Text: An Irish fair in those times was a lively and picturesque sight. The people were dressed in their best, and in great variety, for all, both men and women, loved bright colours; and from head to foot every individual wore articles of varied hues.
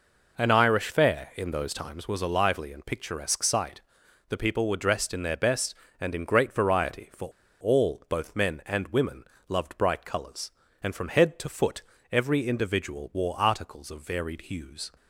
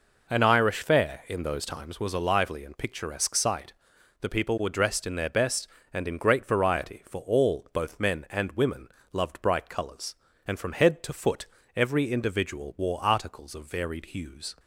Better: second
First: pauses between "for" and "all"; slight; at 7.2 s; 0.31 s long // pauses between "foot" and "every"; slight; at 11.8 s; 0.28 s long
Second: pauses between "foot" and "every"; slight; at 11.4 s; 0.28 s long

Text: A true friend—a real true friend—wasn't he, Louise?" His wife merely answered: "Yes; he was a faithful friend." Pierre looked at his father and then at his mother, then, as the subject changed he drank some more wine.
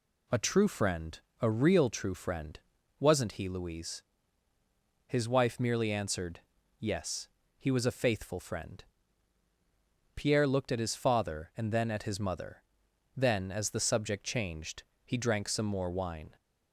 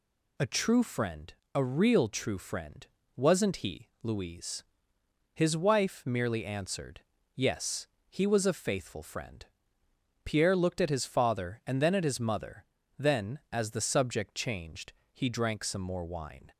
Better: neither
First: pauses between "changed" and "he"; slight; at 14.8 s; 0.22 s long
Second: pauses between "changed" and "he"; slight; at 14.9 s; 0.20 s long

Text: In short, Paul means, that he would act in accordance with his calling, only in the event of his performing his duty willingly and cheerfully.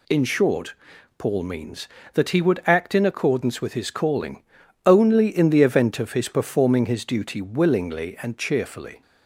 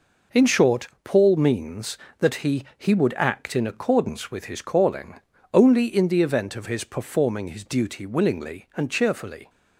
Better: first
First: none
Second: says "he" twice; at 2.7 s

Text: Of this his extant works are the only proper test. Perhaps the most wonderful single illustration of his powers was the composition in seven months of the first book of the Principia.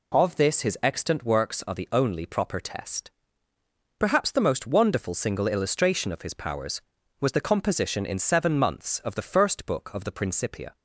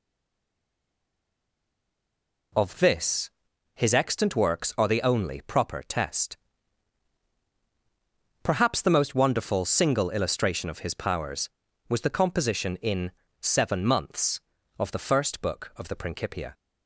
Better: first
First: none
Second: stays silent before the first word; until 2.5 s; 2.5 s long // pauses between "this" and "his"; at 3.3 s; 0.42 s long // pauses between "in" and "seven"; slight; at 13.0 s; 0.32 s long

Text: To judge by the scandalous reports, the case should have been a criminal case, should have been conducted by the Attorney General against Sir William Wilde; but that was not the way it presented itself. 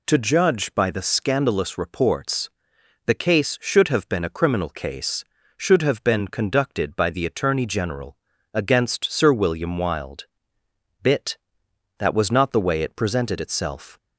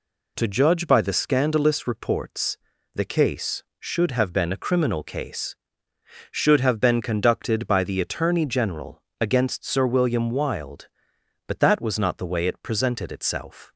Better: second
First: pauses between "General" and "against"; slight; at 8.1 s; 0.36 s long // says "bit" for "but"; at 11.0 s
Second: pauses between "General" and "against"; slight; at 9.0 s; 0.16 s long

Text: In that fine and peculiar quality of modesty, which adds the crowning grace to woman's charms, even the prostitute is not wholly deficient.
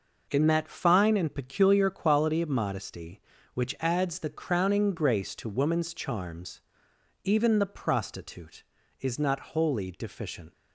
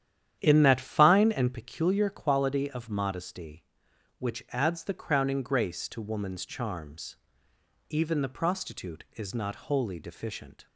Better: first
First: none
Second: starts louder than the rest; strong; until 1.6 s; 10 dB

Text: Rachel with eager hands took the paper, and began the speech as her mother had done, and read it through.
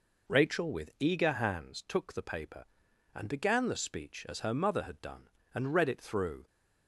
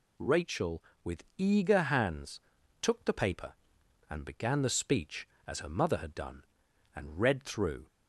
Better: first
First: none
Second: pauses between "with" and "eager"; slight; at 1.2 s; 0.16 s long // pauses between "hands" and "took"; at 2.3 s; 0.42 s long // skips "it"; at 7.4 s

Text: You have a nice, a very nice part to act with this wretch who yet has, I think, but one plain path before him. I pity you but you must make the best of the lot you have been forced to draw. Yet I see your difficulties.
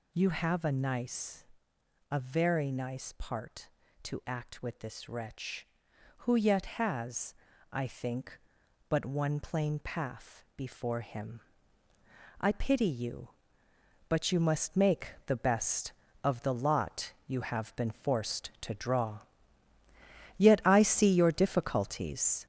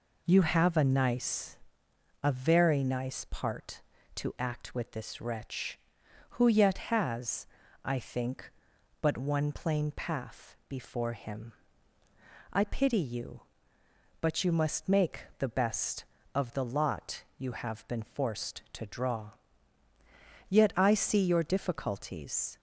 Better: second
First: gets louder; noticeable; throughout; 5.5 dB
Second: none

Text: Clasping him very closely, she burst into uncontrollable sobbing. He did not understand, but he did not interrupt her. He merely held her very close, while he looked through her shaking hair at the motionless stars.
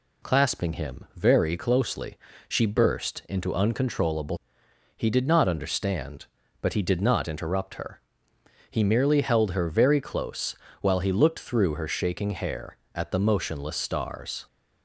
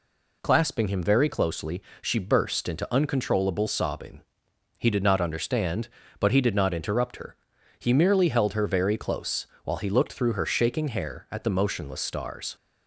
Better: second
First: skips "sobbing"; at 4.6 s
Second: none

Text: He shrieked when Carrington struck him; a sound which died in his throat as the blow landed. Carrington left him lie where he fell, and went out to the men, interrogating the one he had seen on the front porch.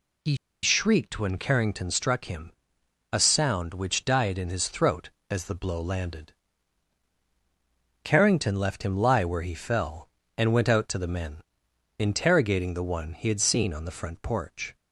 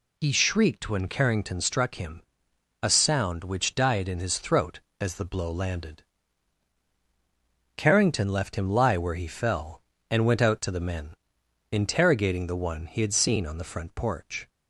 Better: second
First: pauses between "He" and "shrieked"; slight; at 0.3 s; 0.27 s long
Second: none

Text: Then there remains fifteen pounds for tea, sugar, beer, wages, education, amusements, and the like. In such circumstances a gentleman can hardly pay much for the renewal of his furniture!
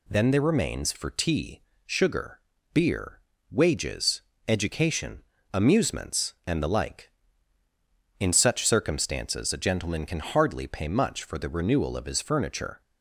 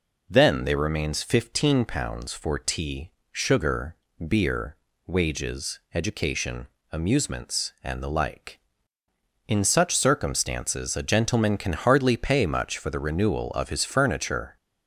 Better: second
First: skips "fifteen pounds"; at 0.9 s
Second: none

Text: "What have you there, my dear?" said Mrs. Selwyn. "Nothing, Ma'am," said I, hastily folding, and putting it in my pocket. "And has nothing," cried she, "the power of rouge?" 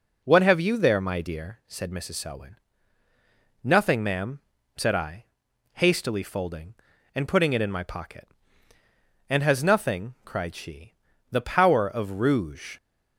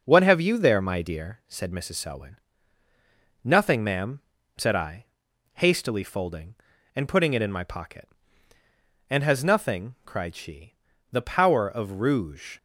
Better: first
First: none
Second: gets quieter; throughout; 3.5 dB

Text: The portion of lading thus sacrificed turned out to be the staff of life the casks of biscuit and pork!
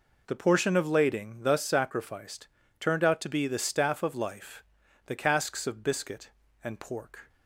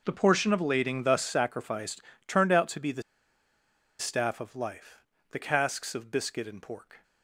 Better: first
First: pauses between "sacrificed" and "turned"; slight; at 2.4 s; 0.32 s long // pauses between "life" and "the"; at 4.6 s; 0.44 s long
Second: pauses between "sacrificed" and "turned"; slight; at 2.0 s; 0.24 s long // pauses between "the" and "staff"; noticeable; at 3.0 s; 0.97 s long // pauses between "life" and "the"; slight; at 4.9 s; 0.34 s long

